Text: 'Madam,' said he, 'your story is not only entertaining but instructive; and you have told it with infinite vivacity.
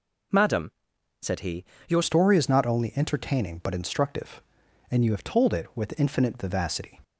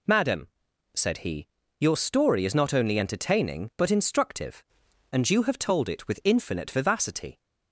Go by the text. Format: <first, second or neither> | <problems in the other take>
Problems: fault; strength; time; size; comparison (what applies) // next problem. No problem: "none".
second | changes voice at "story"; from 2.0 s on; 5.0 s long